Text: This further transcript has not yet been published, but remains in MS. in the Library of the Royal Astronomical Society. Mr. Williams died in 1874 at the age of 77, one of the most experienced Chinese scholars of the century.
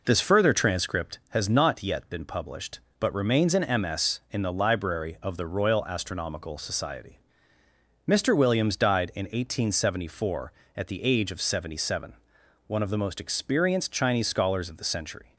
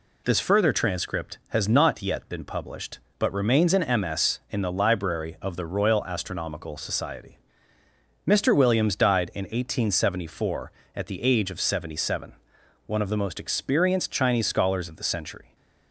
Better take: second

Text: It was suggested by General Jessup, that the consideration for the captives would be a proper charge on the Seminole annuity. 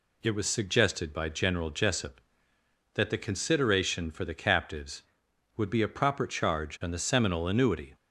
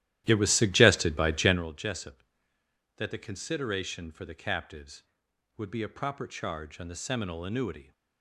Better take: first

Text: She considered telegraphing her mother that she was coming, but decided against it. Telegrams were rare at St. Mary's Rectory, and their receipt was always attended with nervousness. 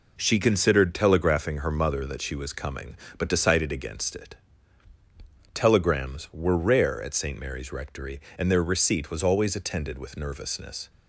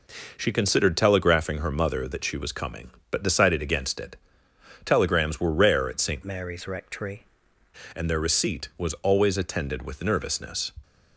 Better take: first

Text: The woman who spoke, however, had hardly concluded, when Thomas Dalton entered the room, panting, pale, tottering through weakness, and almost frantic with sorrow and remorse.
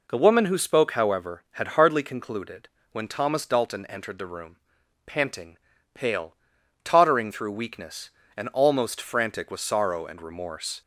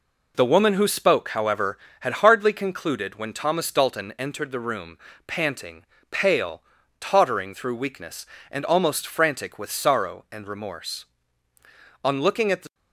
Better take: first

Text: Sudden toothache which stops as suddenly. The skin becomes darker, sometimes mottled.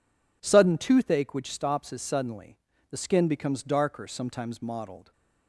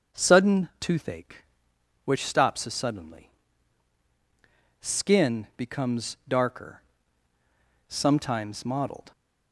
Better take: first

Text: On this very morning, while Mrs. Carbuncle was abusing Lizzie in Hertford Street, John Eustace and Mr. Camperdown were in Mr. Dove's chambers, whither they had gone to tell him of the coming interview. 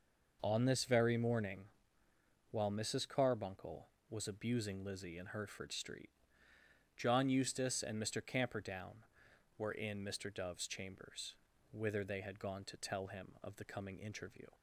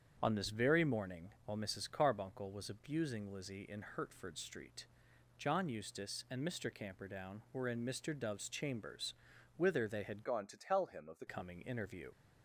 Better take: first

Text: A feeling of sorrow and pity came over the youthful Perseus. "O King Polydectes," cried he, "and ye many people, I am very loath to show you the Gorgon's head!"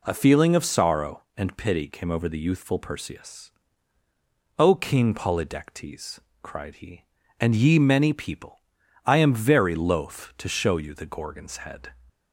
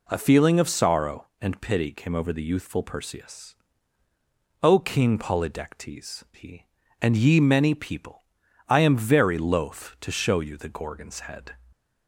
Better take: first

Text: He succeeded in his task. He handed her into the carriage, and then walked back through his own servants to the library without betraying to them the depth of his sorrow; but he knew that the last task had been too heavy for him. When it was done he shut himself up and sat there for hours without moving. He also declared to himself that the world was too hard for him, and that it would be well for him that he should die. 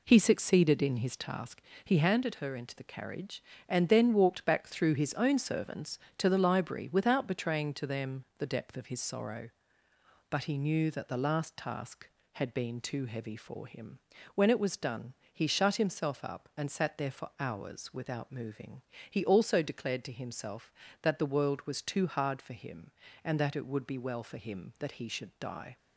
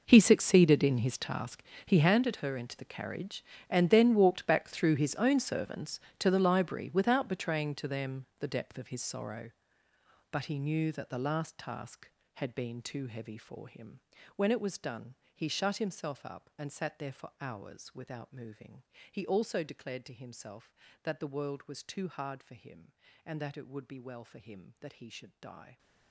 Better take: first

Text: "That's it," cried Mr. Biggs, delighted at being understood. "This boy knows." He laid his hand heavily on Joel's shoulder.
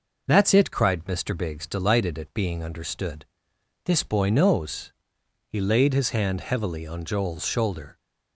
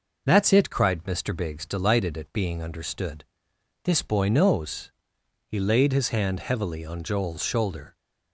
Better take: neither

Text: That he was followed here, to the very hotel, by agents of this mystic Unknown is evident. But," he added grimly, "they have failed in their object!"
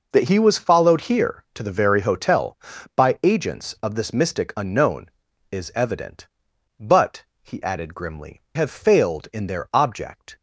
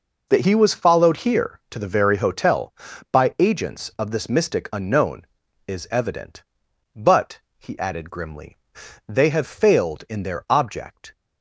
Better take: second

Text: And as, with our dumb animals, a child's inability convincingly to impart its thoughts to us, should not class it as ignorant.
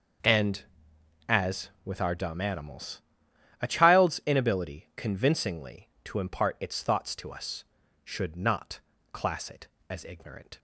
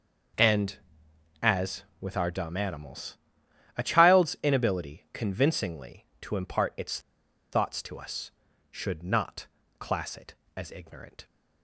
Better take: first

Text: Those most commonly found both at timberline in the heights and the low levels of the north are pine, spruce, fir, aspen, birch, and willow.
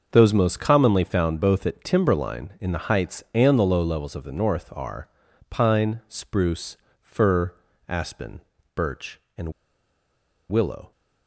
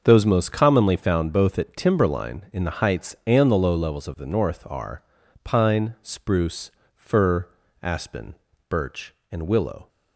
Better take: second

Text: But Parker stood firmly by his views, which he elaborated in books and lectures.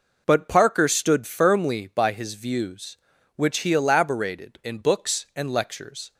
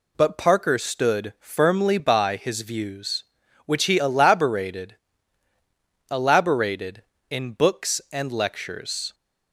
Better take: first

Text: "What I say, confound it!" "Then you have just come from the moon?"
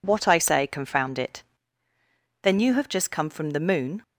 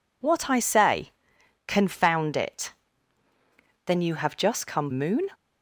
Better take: first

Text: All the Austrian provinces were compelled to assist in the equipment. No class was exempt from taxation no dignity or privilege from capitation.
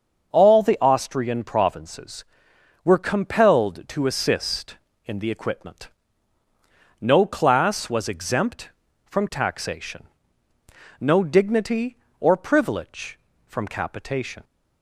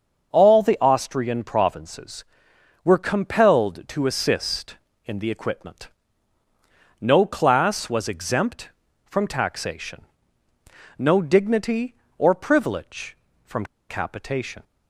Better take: first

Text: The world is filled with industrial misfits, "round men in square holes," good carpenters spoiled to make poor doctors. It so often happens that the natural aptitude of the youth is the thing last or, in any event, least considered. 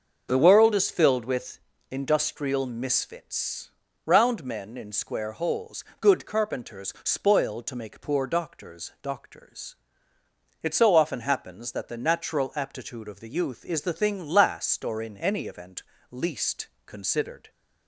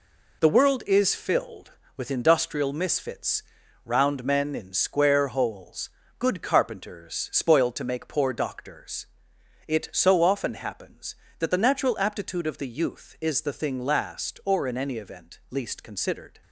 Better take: second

